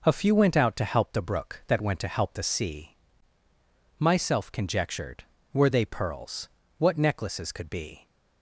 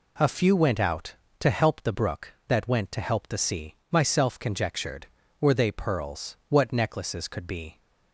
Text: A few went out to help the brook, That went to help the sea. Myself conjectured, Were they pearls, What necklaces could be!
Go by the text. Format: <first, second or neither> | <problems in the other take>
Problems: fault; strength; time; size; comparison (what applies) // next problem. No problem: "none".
neither | none